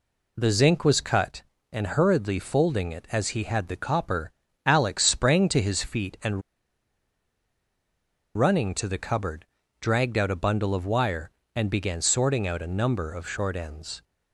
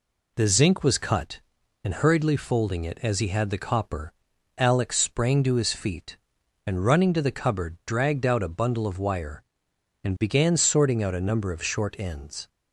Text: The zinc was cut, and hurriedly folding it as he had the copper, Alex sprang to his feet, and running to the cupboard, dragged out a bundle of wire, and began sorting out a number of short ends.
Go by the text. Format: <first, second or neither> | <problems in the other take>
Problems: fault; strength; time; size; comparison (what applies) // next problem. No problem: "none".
second | pauses between "and" and "running"; strong; at 6.4 s; 1.9 s long